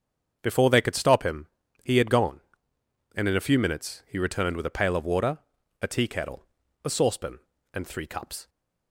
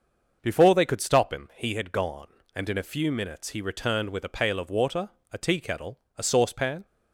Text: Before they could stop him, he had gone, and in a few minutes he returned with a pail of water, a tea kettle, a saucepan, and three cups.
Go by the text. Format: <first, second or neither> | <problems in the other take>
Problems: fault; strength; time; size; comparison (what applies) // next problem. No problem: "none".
first | starts louder than the rest; noticeable; until 1.4 s; 6 dB; also in the first // stops before "and three cups"; at 6.8 s